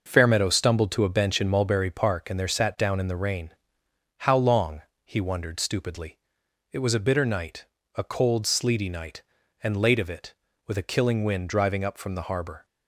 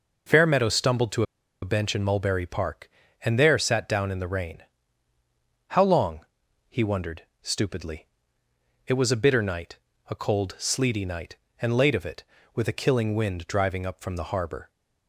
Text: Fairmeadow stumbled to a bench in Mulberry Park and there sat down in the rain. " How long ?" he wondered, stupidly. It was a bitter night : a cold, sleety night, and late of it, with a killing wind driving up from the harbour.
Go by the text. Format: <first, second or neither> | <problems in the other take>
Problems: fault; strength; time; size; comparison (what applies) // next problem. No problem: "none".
first | starts louder than the rest; noticeable; until 1.7 s; 6 dB; also in the first // pauses between "to" and "a"; at 1.2 s; 0.38 s long